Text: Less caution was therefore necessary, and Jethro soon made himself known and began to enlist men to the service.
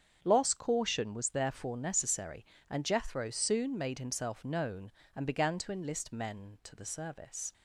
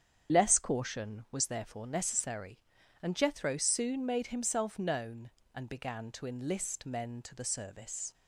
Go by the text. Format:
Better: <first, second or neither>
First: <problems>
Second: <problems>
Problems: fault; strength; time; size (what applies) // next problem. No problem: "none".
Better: second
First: starts louder than the rest; strong; until 1.2 s; 7.5 dB // says "Loss" for "Less"; at 0.2 s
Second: starts louder than the rest; strong; until 1.3 s; 8 dB